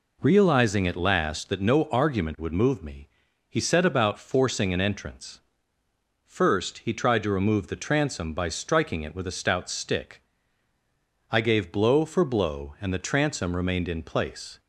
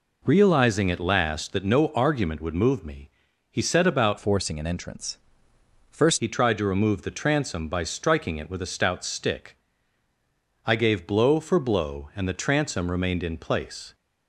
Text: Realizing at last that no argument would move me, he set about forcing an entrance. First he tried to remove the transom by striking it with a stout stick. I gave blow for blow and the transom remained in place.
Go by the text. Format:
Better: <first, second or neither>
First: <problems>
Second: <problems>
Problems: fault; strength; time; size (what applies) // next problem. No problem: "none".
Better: first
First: none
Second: changes voice from "forcing" to "First"; from 4.1 to 6.1 s; 2.0 s long